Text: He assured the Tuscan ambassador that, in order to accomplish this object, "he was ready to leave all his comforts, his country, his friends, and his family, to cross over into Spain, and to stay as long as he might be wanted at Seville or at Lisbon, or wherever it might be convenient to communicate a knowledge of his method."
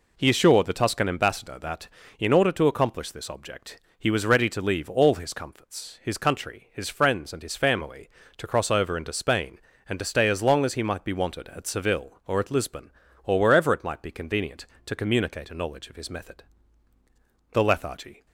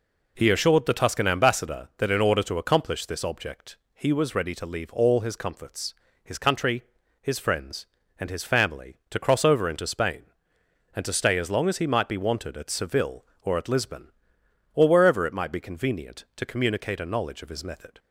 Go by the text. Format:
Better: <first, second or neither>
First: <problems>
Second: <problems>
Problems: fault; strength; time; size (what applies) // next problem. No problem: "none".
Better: second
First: goes on to say "The lethargy"; noticeable; from 17.5 s on; 0.74 s long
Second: none